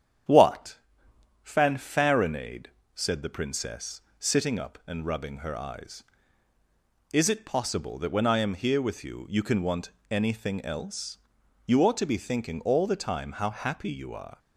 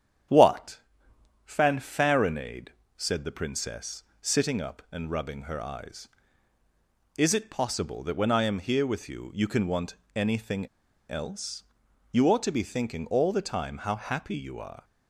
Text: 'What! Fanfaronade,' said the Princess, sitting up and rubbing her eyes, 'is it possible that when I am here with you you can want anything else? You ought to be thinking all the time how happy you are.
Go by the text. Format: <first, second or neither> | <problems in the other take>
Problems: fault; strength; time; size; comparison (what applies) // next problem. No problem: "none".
first | starts louder than the rest; strong; until 1.9 s; 9 dB; strong in the first // pauses between "want" and "anything"; slight; at 9.9 s; 0.20 s long; slight in the first // pauses between "anything" and "else"; at 10.6 s; 0.41 s long